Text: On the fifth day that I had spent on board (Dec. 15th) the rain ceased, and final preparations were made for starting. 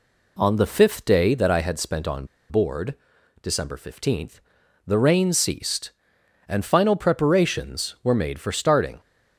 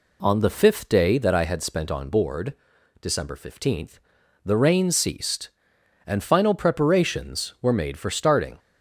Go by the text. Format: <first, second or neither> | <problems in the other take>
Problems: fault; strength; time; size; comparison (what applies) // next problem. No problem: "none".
second | pauses between "on" and "board"; slight; at 2.2 s; 0.23 s long